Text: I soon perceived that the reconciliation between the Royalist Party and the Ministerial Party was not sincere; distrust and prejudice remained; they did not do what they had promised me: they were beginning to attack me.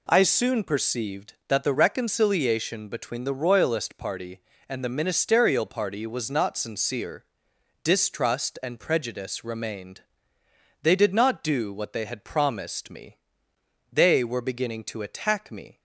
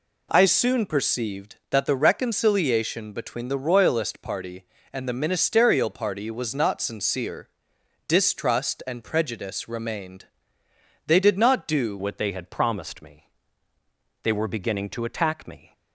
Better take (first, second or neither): first